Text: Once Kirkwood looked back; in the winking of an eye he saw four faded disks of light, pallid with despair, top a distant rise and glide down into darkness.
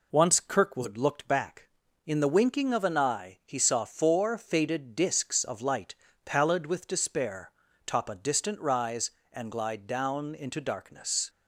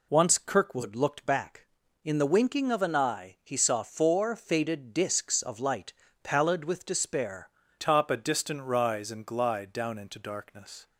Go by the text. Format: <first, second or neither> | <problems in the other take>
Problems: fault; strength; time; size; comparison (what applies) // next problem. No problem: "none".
first | changes voice at "top"; from 7.7 s on; 3.1 s long